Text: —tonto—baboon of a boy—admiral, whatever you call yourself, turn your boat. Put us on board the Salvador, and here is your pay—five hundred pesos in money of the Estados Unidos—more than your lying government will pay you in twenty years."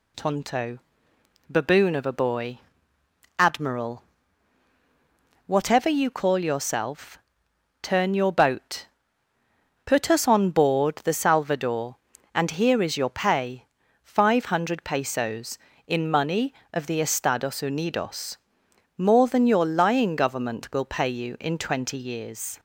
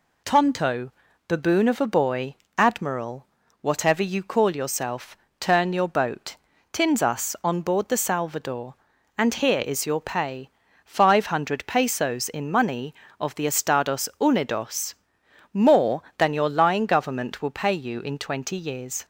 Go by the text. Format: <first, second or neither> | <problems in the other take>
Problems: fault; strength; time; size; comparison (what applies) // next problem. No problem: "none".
first | says "Tins" for "Put"; at 6.7 s